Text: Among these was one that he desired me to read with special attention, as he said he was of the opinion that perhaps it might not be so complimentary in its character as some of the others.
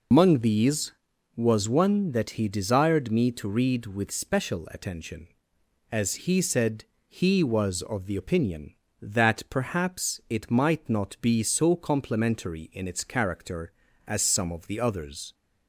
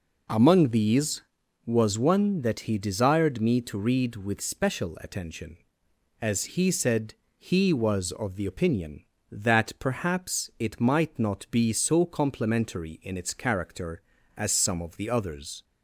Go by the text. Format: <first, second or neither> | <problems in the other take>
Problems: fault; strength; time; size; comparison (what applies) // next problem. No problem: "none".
second | loses the start of "Among"; at 0.1 s; 110 ms // pauses between "said" and "he"; slight; at 6.8 s; 0.24 s long; slight in the second